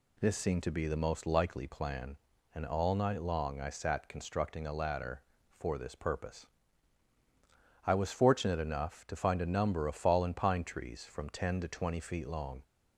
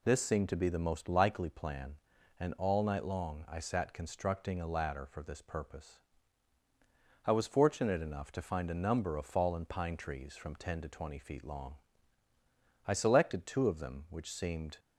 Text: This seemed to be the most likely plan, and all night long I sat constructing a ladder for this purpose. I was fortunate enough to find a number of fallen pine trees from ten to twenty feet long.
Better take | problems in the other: first | goes on to say "I selected two of them which seemed"; strong; from 12.8 s on; 1.9 s long

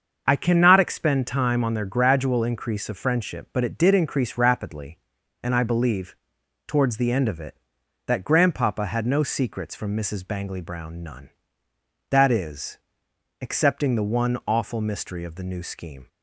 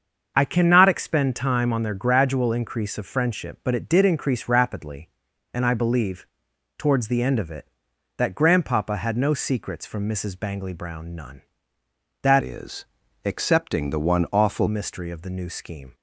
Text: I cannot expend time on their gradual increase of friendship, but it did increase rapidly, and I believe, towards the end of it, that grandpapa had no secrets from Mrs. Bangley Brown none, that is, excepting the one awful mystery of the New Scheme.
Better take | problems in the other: first | starts louder than the rest; until 1.3 s; 6.5 dB; also in the first // changes voice from "is" to "awful"; from 12.4 to 14.6 s; 2.2 s long

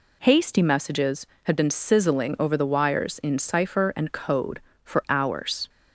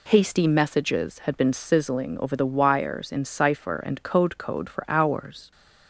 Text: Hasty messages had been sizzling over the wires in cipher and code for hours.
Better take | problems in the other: first | says "code" twice; at 4.3 s

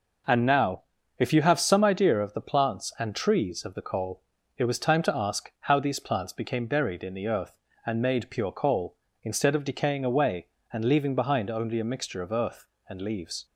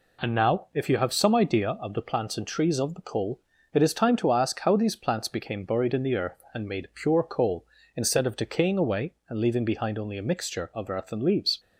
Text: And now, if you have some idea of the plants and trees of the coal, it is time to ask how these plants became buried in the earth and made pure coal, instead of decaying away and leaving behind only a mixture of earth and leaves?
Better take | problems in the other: second | says "was" for "is"; at 4.6 s

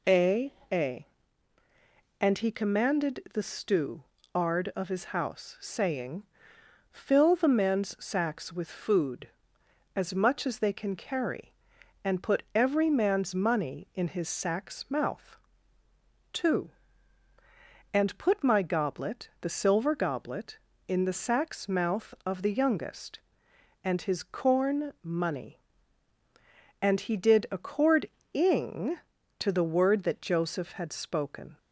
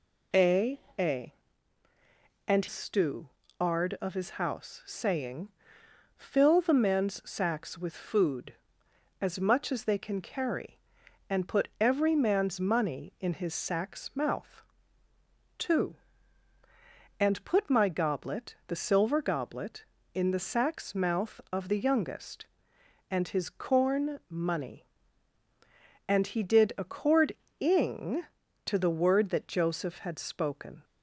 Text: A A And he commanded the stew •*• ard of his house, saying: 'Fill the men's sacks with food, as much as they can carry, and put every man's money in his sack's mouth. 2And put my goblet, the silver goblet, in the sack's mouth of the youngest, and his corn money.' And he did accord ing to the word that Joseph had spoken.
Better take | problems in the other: first | pauses between "A" and "A"; slight; at 0.7 s; 0.20 s long; slight in the first // skips "he commanded the"; at 2.6 s // pauses between "accord" and "ing"; slight; at 27.3 s; 0.24 s long; slight in the first

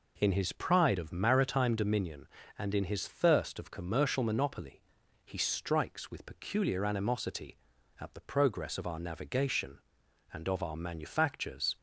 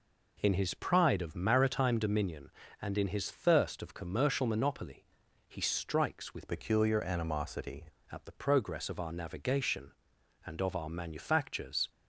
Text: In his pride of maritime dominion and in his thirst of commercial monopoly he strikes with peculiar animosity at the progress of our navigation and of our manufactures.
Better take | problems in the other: first | pauses between "monopoly" and "he"; at 5.0 s; 0.44 s long; also in the first // changes voice from "peculiar" to "animosity"; from 6.4 to 7.8 s; 1.4 s long

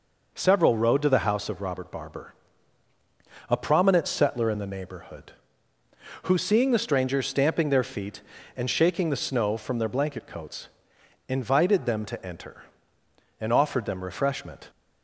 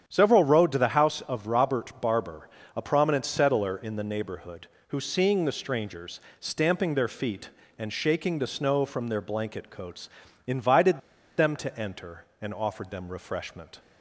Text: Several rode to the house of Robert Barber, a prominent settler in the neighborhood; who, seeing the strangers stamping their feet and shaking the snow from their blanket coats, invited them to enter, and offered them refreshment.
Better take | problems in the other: first | starts louder than the rest; strong; until 1.0 s; 8.5 dB // pauses between "strangers" and "stamping"; slight; at 6.2 s; 0.18 s long // pauses between "invited" and "them"; at 11.0 s; 0.37 s long

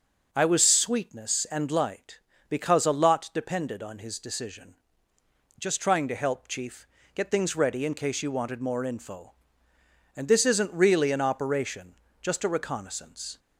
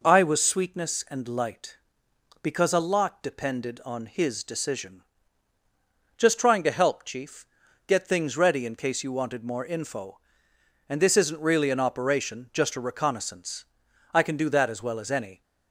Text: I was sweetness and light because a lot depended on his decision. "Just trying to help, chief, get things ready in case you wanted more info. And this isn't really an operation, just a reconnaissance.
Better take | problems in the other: first | goes on to say "I can do that as well as any"; noticeable; from 14.1 s on; 1.2 s long

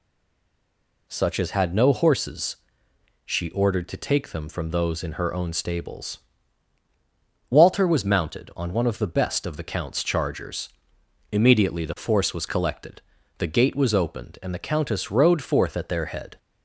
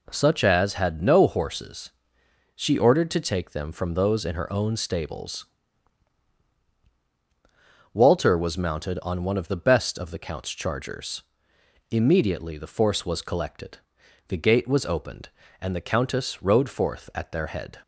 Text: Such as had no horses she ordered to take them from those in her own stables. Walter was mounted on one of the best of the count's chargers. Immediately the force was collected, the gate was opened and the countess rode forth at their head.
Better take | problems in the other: second | stays silent before the first word; until 1.0 s; 1.0 s long // pauses between "horses" and "she"; noticeable; at 2.5 s; 0.72 s long; noticeable in the second

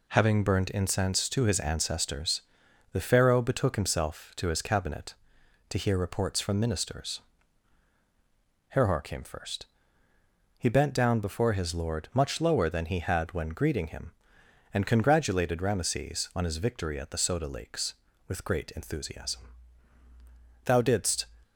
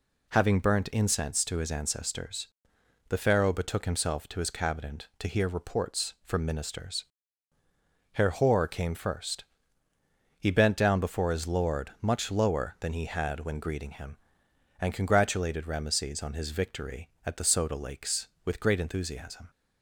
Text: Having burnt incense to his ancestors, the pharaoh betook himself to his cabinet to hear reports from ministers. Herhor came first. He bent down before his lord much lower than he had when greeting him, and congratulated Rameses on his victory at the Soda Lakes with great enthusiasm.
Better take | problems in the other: second | goes on to say "Thou didst"; from 20.6 s on; 0.60 s long

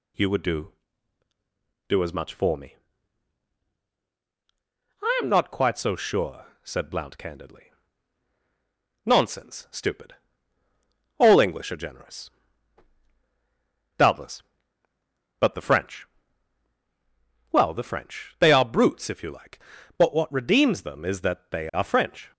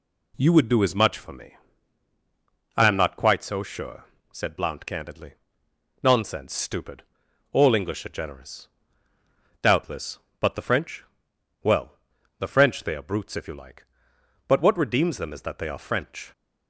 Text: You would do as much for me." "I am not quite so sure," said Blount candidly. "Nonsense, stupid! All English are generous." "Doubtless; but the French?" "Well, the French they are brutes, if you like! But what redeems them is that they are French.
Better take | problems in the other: second | says "do" twice; at 1.8 s

